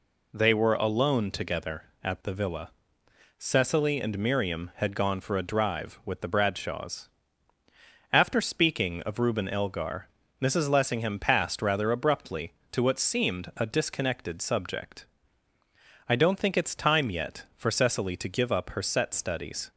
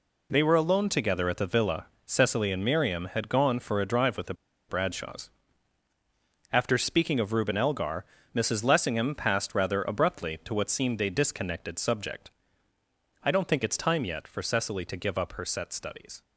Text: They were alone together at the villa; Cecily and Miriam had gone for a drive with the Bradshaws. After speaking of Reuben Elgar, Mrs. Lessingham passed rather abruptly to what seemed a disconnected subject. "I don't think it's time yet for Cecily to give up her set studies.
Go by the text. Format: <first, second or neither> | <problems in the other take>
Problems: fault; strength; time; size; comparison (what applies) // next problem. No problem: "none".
first | pauses between "the" and "Bradshaws"; slight; at 4.3 s; 0.35 s long